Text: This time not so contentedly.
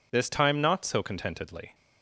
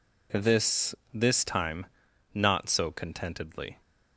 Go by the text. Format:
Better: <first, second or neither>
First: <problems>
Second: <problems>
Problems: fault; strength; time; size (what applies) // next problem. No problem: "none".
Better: first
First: none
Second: says "This" twice; at 1.1 s // pauses between "time" and "not"; noticeable; at 1.8 s; 0.46 s long